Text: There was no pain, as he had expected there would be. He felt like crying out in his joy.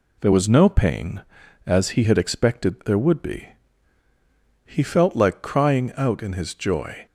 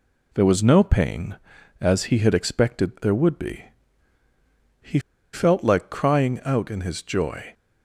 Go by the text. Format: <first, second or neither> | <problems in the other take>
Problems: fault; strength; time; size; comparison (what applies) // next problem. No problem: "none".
first | pauses between "He" and "felt"; slight; at 4.9 s; 0.33 s long